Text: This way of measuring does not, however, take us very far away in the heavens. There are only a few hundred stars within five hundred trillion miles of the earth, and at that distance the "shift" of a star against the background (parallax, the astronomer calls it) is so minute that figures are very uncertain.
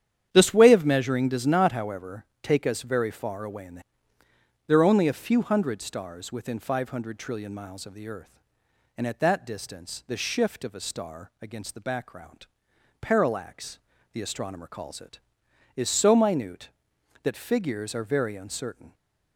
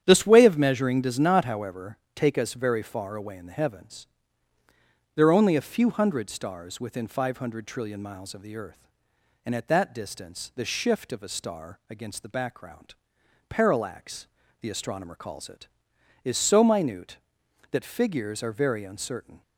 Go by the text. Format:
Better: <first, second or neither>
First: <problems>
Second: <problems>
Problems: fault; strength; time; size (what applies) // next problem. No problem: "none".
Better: second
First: starts louder than the rest; strong; until 1.3 s; 9.5 dB // skips "heavens"; at 4.2 s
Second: starts louder than the rest; strong; until 1.0 s; 9 dB